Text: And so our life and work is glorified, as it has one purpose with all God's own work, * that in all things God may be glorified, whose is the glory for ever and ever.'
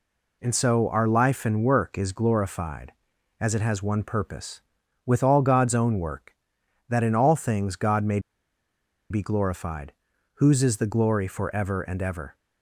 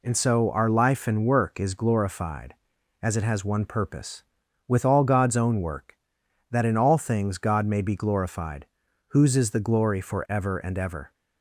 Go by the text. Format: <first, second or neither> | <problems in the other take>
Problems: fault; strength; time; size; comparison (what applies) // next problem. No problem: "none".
second | pauses between "may" and "be"; noticeable; at 8.1 s; 0.91 s long